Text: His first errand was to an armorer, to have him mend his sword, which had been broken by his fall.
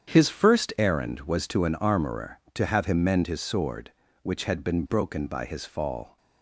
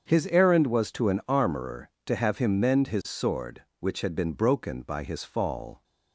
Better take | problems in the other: first | starts louder than the rest; strong; until 1.0 s; 7 dB; strong in the first // skips "first"; at 0.2 s

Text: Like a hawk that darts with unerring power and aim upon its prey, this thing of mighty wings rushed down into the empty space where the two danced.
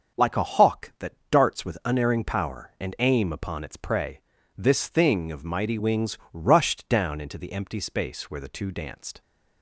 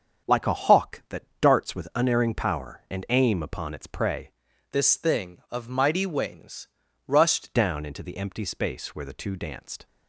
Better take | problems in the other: first | starts louder than the rest; strong; until 1.5 s; 7.5 dB; also in the first // pauses between "that" and "darts"; slight; at 1.2 s; 0.18 s long; slight in the first // changes voice from "this" to "rushed"; from 4.7 to 7.5 s; 2.8 s long // pauses between "wings" and "rushed"; at 6.6 s; 0.38 s long; slight in the first

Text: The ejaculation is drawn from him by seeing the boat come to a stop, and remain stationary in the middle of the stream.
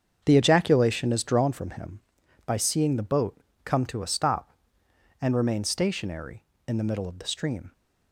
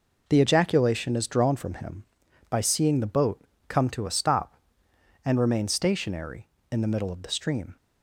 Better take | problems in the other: second | starts louder than the rest; strong; until 1.5 s; 7 dB // pauses between "boat" and "come"; slight; at 3.3 s; 0.28 s long; slight in the second

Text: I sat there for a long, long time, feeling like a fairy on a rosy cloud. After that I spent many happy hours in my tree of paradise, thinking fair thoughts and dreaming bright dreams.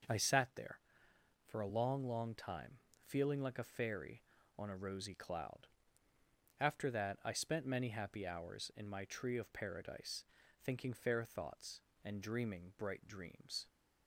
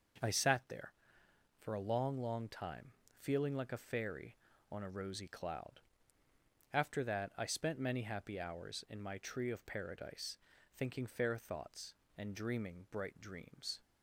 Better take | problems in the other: neither | starts louder than the rest; the same in both

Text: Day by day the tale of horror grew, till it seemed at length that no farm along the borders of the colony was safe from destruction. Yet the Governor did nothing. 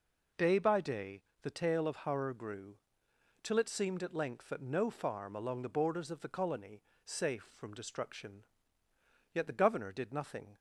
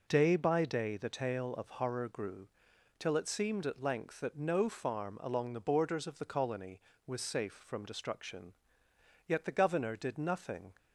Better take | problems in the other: second | pauses between "day" and "the"; slight; at 1.2 s; 0.20 s long // skips "was"; at 6.9 s

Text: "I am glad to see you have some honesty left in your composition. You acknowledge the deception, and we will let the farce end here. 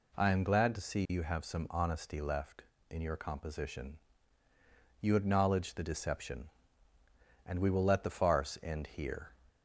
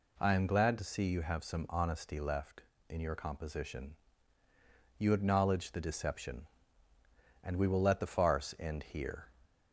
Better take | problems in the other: neither | none

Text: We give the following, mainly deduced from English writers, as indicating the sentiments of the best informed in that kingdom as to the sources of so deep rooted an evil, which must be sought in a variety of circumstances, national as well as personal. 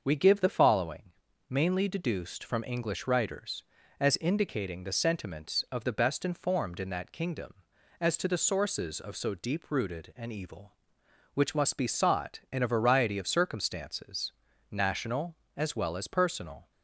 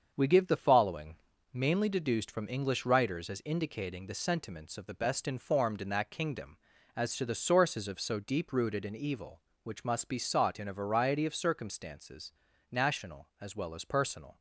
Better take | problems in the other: first | gets quieter; noticeable; throughout; 5.5 dB // starts louder than the rest; until 1.1 s; 7 dB; also in the first

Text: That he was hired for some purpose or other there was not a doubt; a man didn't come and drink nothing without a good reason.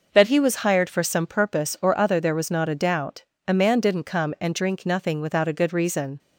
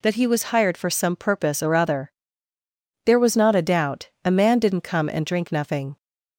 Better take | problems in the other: first | pauses between "other" and "there"; noticeable; at 2.1 s; 0.92 s long // stops before "without a good reason"; at 5.9 s

